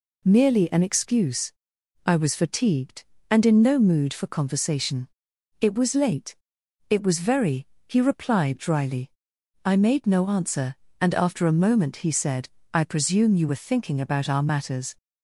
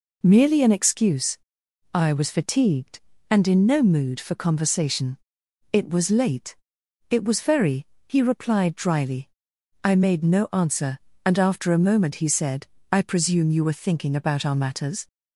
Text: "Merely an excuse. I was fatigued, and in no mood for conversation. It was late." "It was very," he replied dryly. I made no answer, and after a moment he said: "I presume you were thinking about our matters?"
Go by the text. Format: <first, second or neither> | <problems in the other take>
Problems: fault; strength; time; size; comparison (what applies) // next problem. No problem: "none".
neither | none